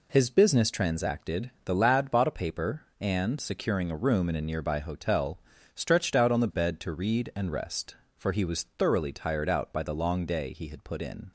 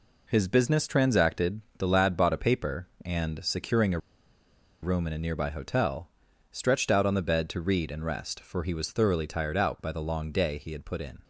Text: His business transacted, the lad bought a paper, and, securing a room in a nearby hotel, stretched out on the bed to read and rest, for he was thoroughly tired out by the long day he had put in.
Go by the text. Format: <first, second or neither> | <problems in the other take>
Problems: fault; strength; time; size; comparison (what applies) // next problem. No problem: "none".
first | pauses between "a" and "room"; noticeable; at 3.9 s; 0.83 s long